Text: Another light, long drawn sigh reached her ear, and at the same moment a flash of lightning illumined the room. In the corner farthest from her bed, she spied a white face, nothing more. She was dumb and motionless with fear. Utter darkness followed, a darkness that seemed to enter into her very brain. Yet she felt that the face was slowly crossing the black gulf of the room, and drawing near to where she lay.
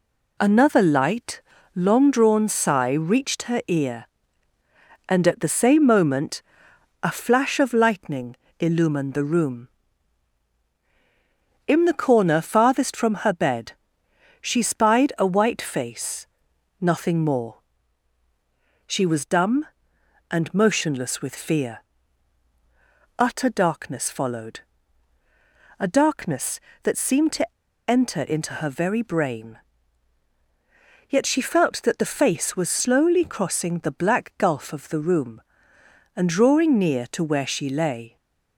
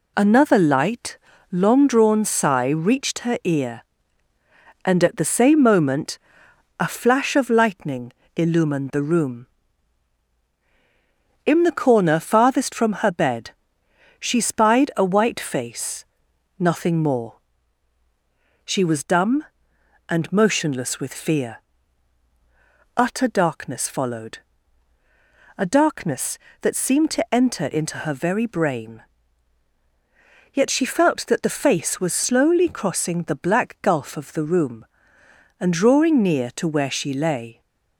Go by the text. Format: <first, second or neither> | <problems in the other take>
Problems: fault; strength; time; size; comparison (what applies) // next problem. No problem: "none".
second | pauses between "moment" and "a"; noticeable; at 6.4 s; 0.58 s long; noticeable in the second // pauses between "lightning" and "illumined"; slight; at 8.3 s; 0.24 s long; slight in the second // pauses between "to" and "enter"; at 27.5 s; 0.36 s long